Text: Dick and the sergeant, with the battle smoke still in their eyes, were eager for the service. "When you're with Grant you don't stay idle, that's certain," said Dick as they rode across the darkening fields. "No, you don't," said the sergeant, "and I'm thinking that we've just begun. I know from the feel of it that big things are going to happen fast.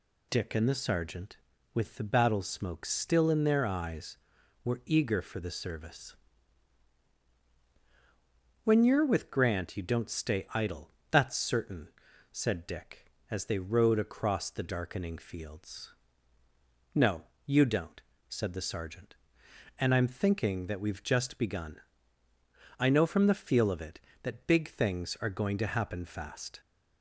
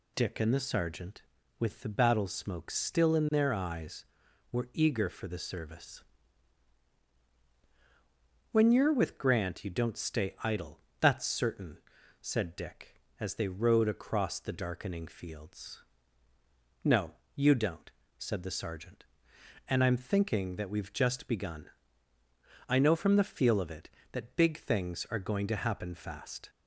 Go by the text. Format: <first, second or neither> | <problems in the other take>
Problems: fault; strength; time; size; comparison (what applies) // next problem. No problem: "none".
neither | none